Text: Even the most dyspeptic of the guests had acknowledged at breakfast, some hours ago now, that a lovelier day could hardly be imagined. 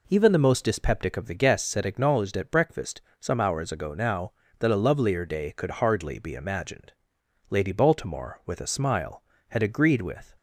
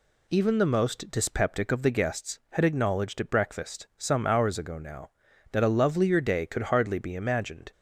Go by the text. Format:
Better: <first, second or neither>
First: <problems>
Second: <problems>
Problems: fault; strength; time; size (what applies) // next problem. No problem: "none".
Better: second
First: goes on to say "Lady Baltimore with a smile had agreed with"; strong; from 7.4 s on; 2.8 s long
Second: none